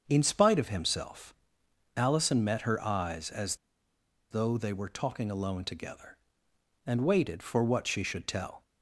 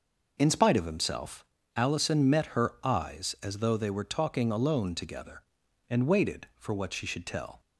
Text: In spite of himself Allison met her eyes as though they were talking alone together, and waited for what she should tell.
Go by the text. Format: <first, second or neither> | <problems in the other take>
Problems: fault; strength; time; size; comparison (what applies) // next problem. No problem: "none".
second | starts louder than the rest; until 1.0 s; 7 dB // pauses between "himself" and "Allison"; noticeable; at 1.3 s; 0.64 s long; slight in the second // pauses between "as" and "though"; noticeable; at 3.5 s; 0.75 s long